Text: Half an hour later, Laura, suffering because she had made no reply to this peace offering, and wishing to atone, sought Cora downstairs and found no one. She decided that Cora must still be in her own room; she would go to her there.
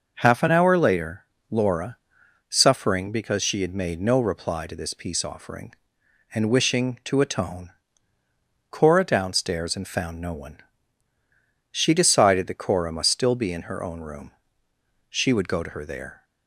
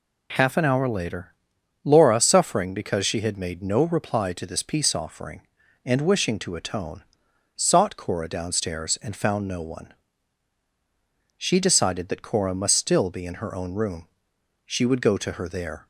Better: second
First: skips "sought"; at 8.2 s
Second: none

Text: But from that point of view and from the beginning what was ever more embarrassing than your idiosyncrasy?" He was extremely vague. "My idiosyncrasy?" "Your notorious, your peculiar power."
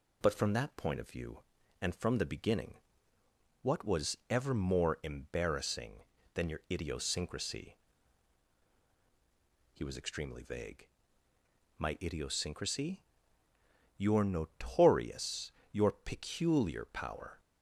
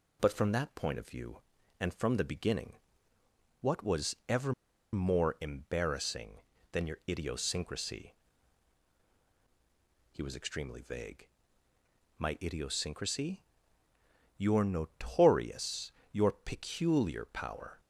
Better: first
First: pauses between "beginning" and "what"; noticeable; at 2.7 s; 0.88 s long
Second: pauses between "beginning" and "what"; noticeable; at 2.7 s; 0.88 s long // pauses between "ever" and "more"; at 4.5 s; 0.40 s long

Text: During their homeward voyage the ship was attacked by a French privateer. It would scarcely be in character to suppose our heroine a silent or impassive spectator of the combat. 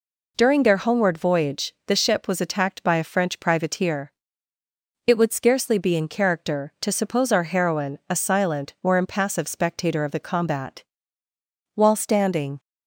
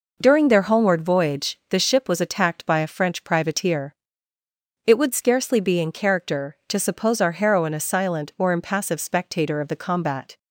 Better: second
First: goes on to say "While standing"; noticeable; from 11.7 s on; 0.86 s long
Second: none

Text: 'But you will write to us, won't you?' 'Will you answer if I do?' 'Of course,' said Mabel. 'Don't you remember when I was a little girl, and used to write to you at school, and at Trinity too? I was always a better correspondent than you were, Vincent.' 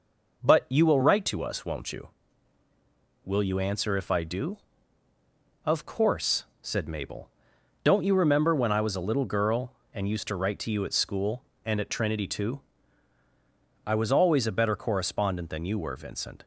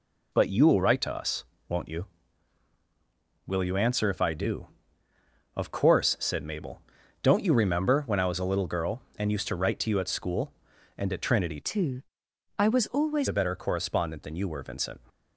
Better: first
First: none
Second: changes voice from "too" to "always"; from 11.6 to 13.2 s; 1.6 s long

